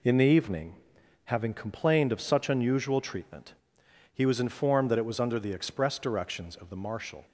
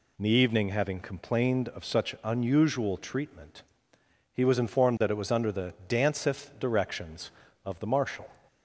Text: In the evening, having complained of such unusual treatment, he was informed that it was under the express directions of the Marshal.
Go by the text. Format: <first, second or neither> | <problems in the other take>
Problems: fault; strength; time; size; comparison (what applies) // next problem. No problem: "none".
first | says "danceth" for "express"; at 5.8 s